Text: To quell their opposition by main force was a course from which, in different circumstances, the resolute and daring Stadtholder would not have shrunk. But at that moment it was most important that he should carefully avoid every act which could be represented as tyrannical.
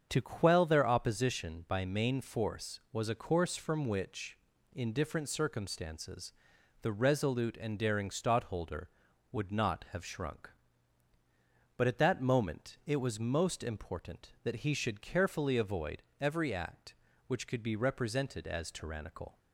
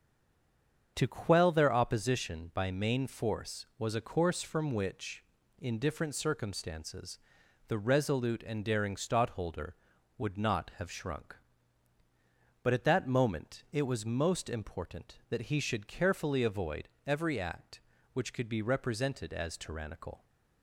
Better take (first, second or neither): first